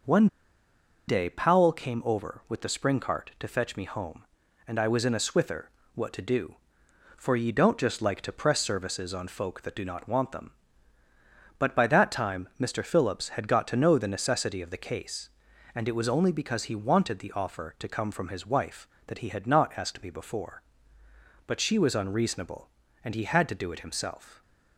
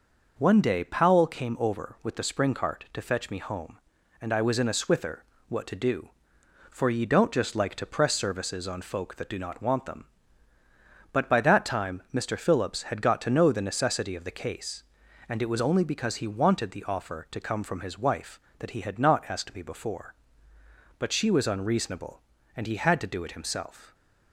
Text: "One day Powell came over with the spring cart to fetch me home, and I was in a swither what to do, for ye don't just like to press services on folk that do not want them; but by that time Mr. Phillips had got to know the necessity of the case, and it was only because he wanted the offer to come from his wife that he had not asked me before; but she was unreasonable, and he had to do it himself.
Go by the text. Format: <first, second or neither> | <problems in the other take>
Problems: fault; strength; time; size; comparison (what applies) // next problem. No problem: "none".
second | pauses between "One" and "day"; noticeable; at 0.2 s; 0.80 s long // pauses between "swither" and "what"; slight; at 5.6 s; 0.24 s long; slight in the second